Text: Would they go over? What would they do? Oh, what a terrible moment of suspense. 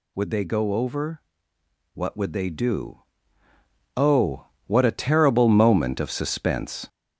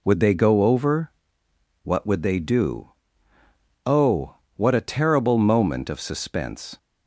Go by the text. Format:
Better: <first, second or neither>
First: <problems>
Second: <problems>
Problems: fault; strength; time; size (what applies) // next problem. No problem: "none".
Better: second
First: gets louder; noticeable; throughout; 5.5 dB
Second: none